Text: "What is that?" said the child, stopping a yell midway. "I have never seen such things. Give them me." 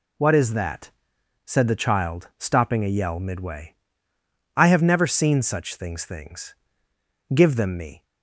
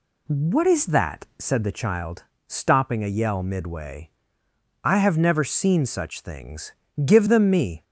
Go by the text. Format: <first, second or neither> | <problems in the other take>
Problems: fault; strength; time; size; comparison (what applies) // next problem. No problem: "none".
second | says "things" twice; at 6.0 s